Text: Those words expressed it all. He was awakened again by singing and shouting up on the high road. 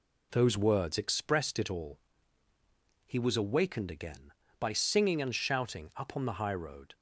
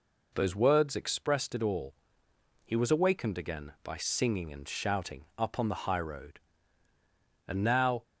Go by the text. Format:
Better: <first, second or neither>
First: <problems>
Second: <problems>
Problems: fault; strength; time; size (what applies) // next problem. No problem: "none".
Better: first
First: none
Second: goes on to say "And now"; from 7.4 s on; 0.56 s long